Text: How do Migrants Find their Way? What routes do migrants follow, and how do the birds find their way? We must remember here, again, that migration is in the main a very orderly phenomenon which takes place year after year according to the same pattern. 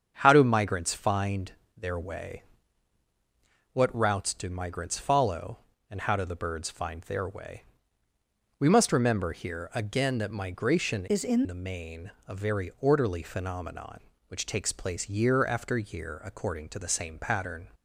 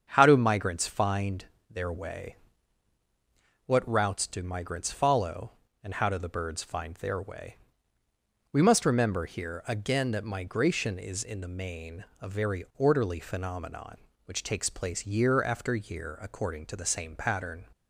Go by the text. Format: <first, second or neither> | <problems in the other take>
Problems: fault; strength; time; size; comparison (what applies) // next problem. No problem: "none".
second | starts louder than the rest; strong; until 1.2 s; 7.5 dB; strong in the second // pauses between "Find" and "their"; slight; at 1.5 s; 0.24 s long; slight in the second // changes voice from "is" to "in"; from 11.0 to 11.4 s; 0.4 s long // pauses between "main" and "a"; slight; at 12.1 s; 0.18 s long; slight in the second